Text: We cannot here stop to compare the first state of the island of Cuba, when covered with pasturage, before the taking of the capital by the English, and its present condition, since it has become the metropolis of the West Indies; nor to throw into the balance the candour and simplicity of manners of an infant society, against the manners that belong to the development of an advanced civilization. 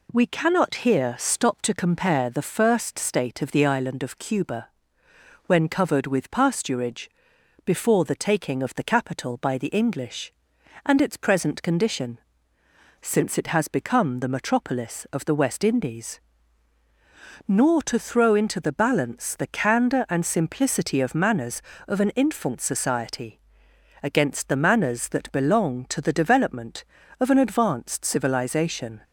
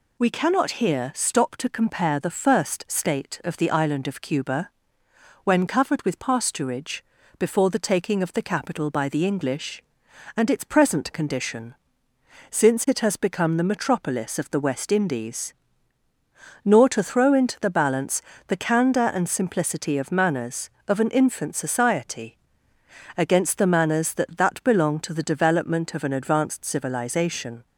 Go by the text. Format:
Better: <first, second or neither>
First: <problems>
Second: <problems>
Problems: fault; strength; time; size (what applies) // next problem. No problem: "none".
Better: first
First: none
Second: pauses between "balance" and "the"; slight; at 18.2 s; 0.26 s long // says "that" twice; at 24.3 s